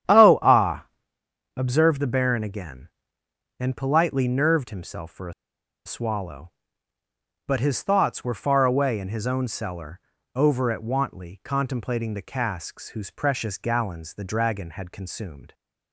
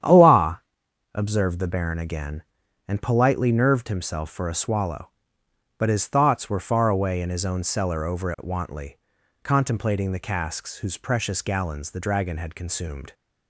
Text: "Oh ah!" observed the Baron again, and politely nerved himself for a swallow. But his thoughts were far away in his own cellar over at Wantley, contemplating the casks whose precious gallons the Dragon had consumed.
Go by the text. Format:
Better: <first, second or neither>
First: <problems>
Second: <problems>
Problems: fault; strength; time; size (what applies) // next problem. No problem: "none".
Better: second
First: starts louder than the rest; strong; until 1.8 s; 10.5 dB // pauses between "a" and "swallow"; noticeable; at 5.3 s; 0.52 s long // pauses between "cellar" and "over"; slight; at 9.9 s; 0.34 s long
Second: starts louder than the rest; strong; until 1.5 s; 9.5 dB